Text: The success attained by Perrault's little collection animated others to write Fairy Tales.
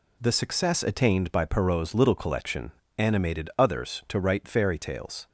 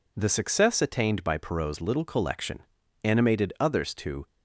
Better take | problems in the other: first | pauses between "collection" and "animated"; at 2.6 s; 0.40 s long; slight in the first // stops before "write Fairy Tales"; at 4.2 s

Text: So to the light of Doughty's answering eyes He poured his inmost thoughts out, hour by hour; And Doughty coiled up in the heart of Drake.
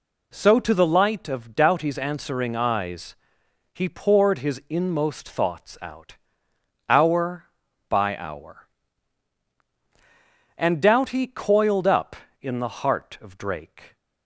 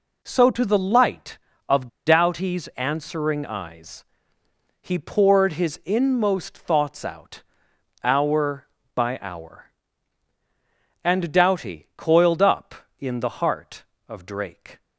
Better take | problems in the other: first | pauses between "of" and "Doughty's"; slight; at 1.8 s; 0.19 s long // pauses between "eyes" and "He"; noticeable; at 4.0 s; 0.76 s long; noticeable in the first

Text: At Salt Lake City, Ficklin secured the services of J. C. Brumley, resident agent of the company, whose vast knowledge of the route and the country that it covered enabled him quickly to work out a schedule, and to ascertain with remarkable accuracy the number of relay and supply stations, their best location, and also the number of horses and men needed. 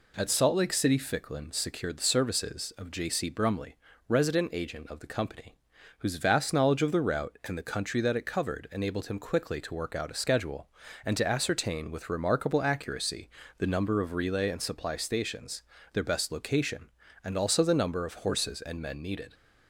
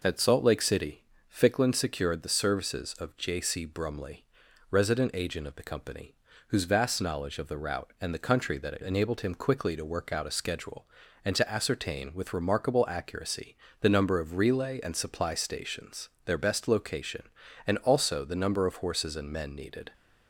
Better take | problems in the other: first | skips "covered"; at 8.8 s // pauses between "accuracy" and "the"; slight; at 13.5 s; 0.24 s long; slight in the first

